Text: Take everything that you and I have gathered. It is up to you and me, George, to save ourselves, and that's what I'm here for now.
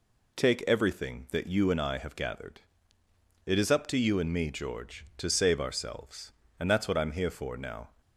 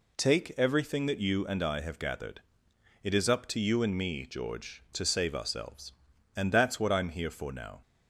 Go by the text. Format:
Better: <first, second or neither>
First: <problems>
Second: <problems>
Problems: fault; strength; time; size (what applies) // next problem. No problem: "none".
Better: neither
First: none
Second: none